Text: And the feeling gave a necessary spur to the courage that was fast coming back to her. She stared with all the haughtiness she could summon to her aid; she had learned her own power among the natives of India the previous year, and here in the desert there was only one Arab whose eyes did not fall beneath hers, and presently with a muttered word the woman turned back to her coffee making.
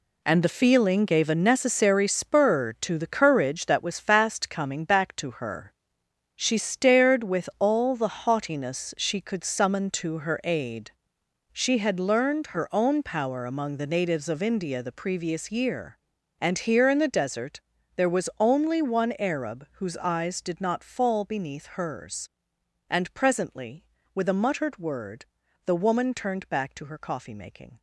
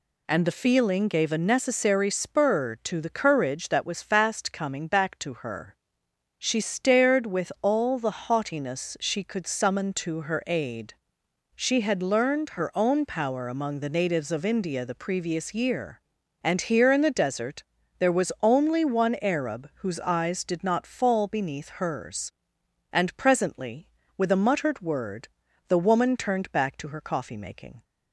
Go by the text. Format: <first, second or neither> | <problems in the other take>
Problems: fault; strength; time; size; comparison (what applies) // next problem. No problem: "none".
second | gets quieter; strong; throughout; 10 dB // pauses between "desert" and "there"; slight; at 17.6 s; 0.36 s long; slight in the second // pauses between "word" and "the"; at 25.2 s; 0.40 s long; also in the second